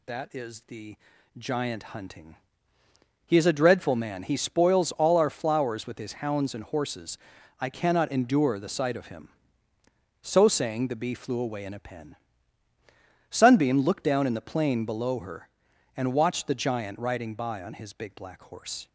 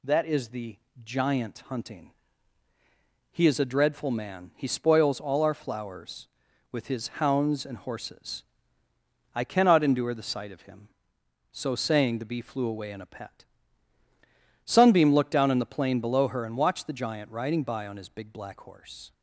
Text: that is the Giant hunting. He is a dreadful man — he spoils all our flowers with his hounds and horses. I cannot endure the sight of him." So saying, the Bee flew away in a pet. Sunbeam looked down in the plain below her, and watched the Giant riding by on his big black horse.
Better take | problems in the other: second | pauses between "the" and "Giant"; at 0.9 s; 0.42 s long; slight in the second // says "pen" for "pet"; at 11.7 s

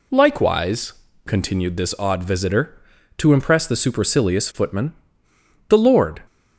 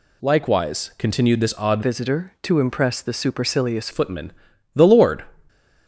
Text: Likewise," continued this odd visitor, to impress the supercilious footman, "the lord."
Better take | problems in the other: first | changes voice from "visitor" to "supercilious"; from 1.8 to 3.8 s; 2.0 s long

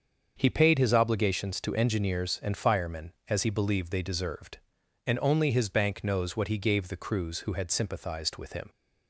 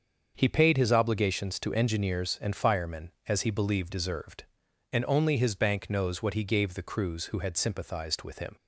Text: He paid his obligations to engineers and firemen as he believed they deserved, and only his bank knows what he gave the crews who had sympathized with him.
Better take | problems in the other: first | starts louder than the rest; until 1.3 s; 6.5 dB; also in the first // skips "they"; at 3.8 s

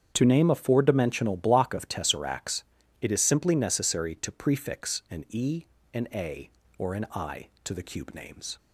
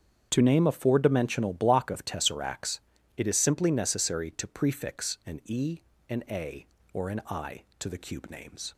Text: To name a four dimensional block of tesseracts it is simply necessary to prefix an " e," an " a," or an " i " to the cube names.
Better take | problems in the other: neither | starts louder than the rest; strong; the same in both // pauses between "tesseracts" and "it"; the same in both

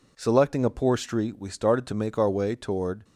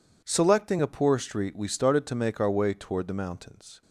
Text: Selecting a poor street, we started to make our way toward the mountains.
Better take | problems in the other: second | stops before "the mountains"; at 3.0 s

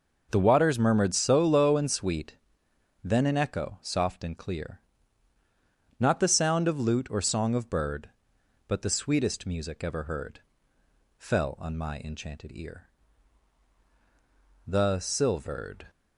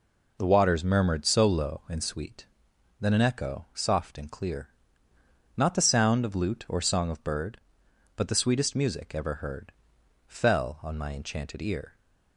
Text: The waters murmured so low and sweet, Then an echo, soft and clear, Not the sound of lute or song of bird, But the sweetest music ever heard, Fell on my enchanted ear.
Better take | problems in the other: second | goes on to say "The silvered"; noticeable; from 14.6 s on; 1.2 s long

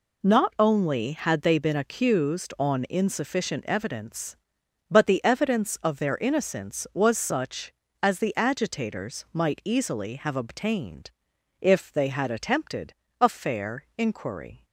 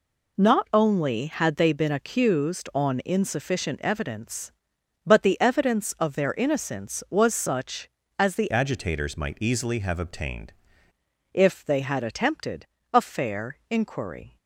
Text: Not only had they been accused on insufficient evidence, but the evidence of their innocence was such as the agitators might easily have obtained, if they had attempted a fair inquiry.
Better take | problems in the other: first | changes voice from "agitators" to "obtained"; from 8.5 to 10.5 s; 2.0 s long // pauses between "attempted" and "a"; slight; at 12.6 s; 0.26 s long; slight in the first

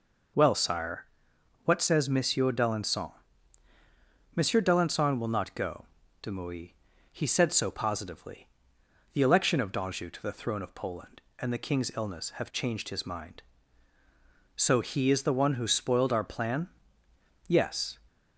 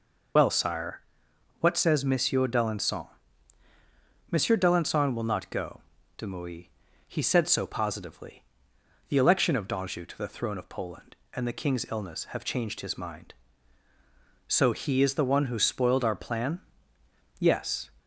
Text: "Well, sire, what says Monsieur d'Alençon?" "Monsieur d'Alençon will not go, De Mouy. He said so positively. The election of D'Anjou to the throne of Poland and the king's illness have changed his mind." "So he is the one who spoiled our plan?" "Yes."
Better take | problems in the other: first | loses the start of "Well"; at 0.3 s; 45 ms

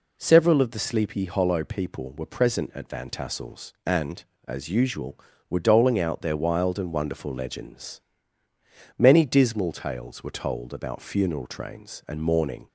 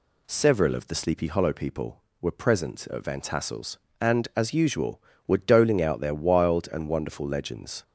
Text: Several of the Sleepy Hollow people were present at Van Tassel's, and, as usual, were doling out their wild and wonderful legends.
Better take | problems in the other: second | goes on to say "Many dismal tales were told about funeral trains and mourning"; strong; from 8.9 s on; 3.7 s long

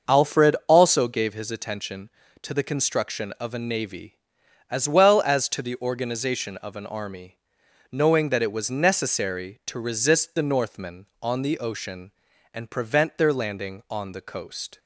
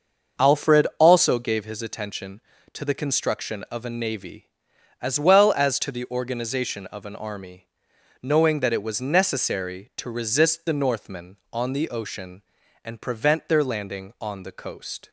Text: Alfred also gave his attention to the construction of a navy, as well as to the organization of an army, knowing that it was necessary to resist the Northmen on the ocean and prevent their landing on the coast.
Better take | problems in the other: neither | starts louder than the rest; the same in both

